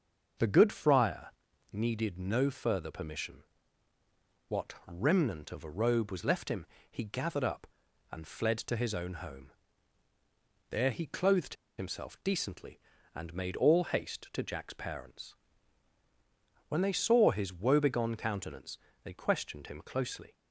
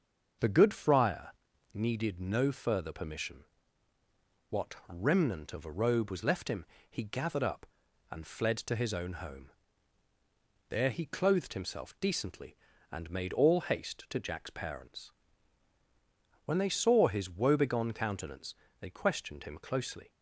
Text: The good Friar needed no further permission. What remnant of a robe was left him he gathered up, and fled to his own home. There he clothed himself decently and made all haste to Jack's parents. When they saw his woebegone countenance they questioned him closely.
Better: second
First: starts louder than the rest; until 1.8 s; 6.5 dB // pauses between "Friar" and "needed"; at 1.2 s; 0.44 s long // pauses between "him" and "he"; slight; at 6.6 s; 0.24 s long // pauses between "clothed" and "himself"; slight; at 11.5 s; 0.22 s long // pauses between "countenance" and "they"; slight; at 18.7 s; 0.26 s long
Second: starts louder than the rest; until 1.8 s; 6.5 dB // pauses between "Friar" and "needed"; at 1.3 s; 0.44 s long // pauses between "him" and "he"; slight; at 6.6 s; 0.24 s long // pauses between "countenance" and "they"; slight; at 18.5 s; 0.26 s long

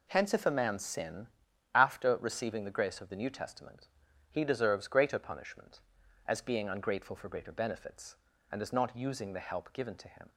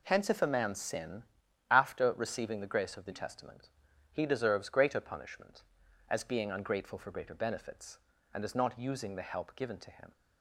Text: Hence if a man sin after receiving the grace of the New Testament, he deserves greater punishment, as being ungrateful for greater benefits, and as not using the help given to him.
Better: first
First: pauses between "sin" and "after"; noticeable; at 1.2 s; 0.48 s long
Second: pauses between "sin" and "after"; noticeable; at 1.2 s; 0.48 s long // skips "New"; at 3.1 s

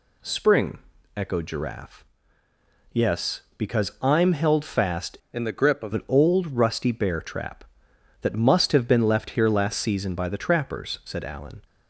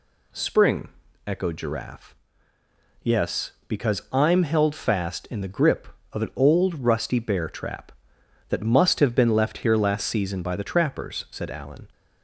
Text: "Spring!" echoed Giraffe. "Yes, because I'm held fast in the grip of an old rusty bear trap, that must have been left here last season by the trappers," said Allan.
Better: second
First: changes voice from "in" to "of"; from 5.3 to 5.9 s; 0.6 s long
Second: none

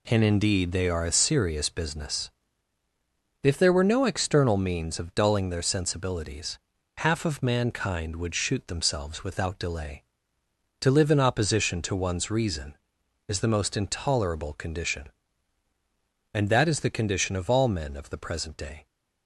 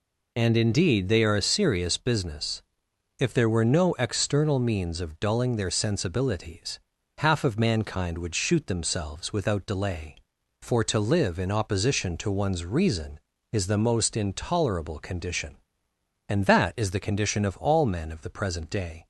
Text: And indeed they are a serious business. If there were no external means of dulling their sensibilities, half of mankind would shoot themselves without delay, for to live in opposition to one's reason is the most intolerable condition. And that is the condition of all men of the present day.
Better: second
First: skips "for"; at 10.4 s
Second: none

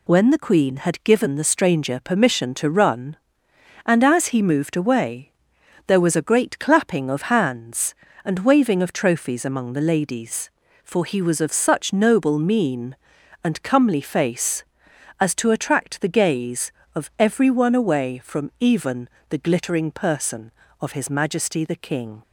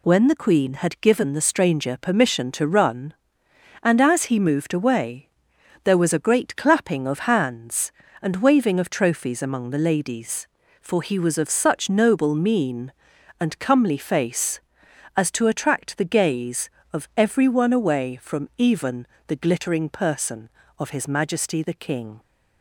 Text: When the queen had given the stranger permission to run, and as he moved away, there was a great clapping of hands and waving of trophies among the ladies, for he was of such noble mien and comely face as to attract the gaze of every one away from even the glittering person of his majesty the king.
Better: neither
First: pauses between "even" and "the"; slight; at 19.0 s; 0.22 s long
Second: pauses between "even" and "the"; slight; at 19.0 s; 0.22 s long

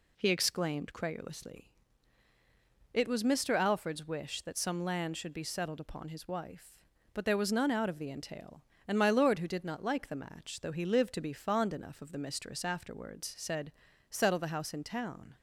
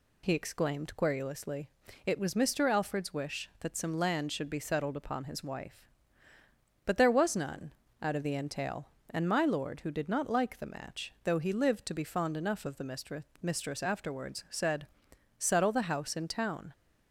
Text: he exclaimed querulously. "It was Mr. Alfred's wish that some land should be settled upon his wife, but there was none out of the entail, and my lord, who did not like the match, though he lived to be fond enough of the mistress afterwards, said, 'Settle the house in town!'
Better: first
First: none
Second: pauses between "none" and "out"; slight; at 7.7 s; 0.28 s long // says "mistress" twice; at 13.4 s

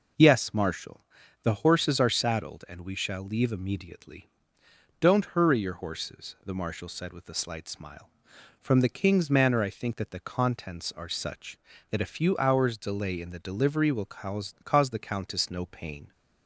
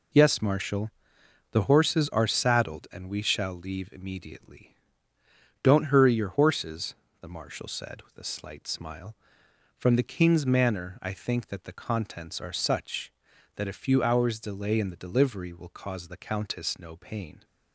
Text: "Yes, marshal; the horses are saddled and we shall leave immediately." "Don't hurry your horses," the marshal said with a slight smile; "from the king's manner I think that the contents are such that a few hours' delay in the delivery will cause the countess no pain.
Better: second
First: says "cause" twice; at 14.6 s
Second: none

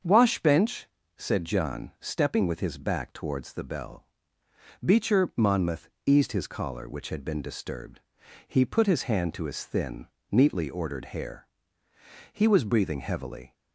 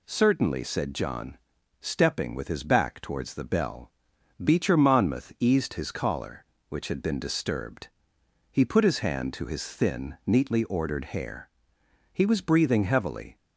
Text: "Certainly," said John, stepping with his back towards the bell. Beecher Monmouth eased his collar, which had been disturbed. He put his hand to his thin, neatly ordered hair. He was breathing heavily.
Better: second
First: starts louder than the rest; until 1.3 s; 7 dB // says "Washbench" for "Certainly"; at 0.0 s // pauses between "Monmouth" and "eased"; slight; at 5.8 s; 0.18 s long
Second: none

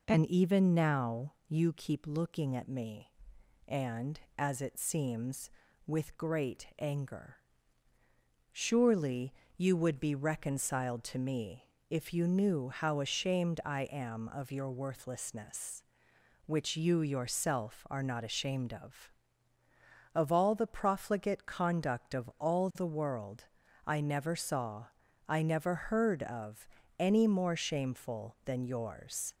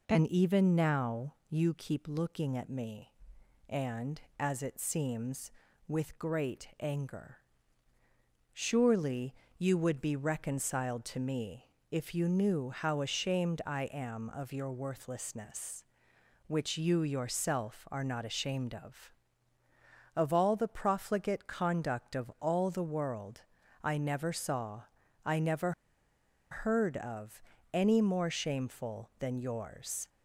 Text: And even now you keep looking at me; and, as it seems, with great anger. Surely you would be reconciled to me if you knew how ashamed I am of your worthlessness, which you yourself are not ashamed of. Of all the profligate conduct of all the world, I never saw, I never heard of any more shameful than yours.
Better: first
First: pauses between "now" and "you"; slight; at 1.3 s; 0.16 s long // pauses between "Surely" and "you"; slight; at 9.3 s; 0.24 s long // pauses between "me" and "if"; slight; at 11.6 s; 0.26 s long // pauses between "of" and "any"; slight; at 26.6 s; 0.32 s long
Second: pauses between "now" and "you"; slight; at 1.3 s; 0.16 s long // pauses between "Surely" and "you"; slight; at 9.3 s; 0.24 s long // pauses between "me" and "if"; slight; at 11.6 s; 0.26 s long // pauses between "never" and "heard"; noticeable; at 25.7 s; 0.80 s long // pauses between "of" and "any"; slight; at 27.4 s; 0.32 s long

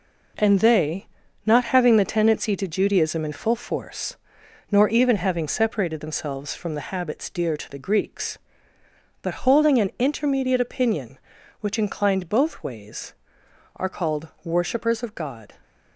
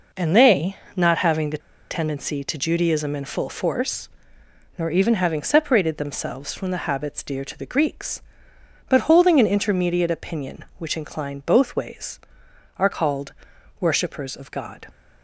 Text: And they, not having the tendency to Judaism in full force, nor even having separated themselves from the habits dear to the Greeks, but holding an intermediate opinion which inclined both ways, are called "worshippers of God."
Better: first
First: none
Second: pauses between "the" and "tendency"; slight; at 1.5 s; 0.31 s long // pauses between "called" and "worshippers"; noticeable; at 13.3 s; 0.46 s long

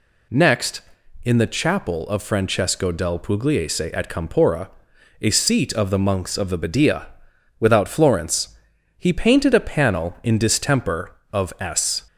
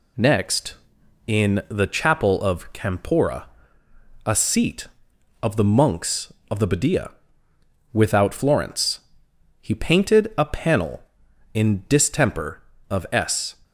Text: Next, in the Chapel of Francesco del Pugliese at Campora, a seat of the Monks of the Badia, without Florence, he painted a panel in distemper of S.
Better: first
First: none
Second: skips "Francesco del Pugliese at"; at 2.7 s

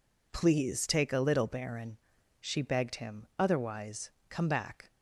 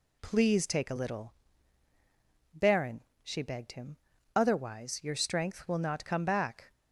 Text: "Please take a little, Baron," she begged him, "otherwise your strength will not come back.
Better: second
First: skips "your strength will not"; at 4.1 s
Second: none

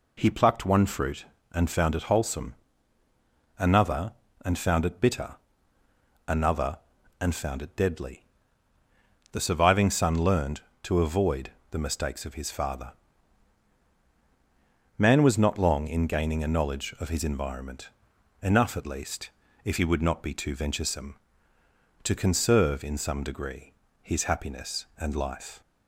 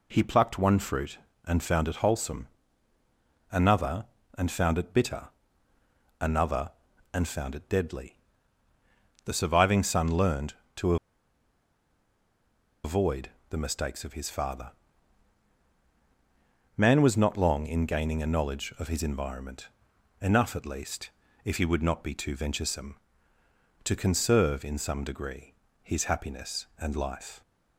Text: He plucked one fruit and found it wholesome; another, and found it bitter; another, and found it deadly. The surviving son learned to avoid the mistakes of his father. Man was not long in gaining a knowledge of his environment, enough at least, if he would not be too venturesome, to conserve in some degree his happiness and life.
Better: first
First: pauses between "avoid" and "the"; slight; at 11.5 s; 0.20 s long // pauses between "degree" and "his"; slight; at 23.7 s; 0.26 s long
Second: pauses between "to" and "avoid"; strong; at 10.9 s; 1.8 s long // pauses between "avoid" and "the"; slight; at 13.2 s; 0.20 s long // pauses between "degree" and "his"; slight; at 25.5 s; 0.26 s long

